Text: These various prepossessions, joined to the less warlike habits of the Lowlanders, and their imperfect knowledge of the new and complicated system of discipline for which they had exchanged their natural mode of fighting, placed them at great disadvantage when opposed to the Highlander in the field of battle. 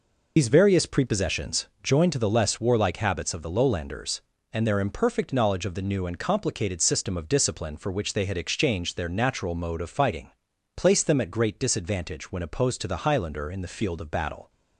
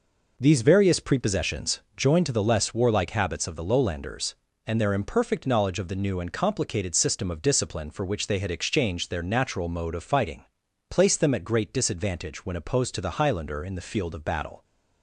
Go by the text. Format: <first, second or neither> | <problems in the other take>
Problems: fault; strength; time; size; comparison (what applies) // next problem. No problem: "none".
second | loses the start of "These"; at 0.3 s; 110 ms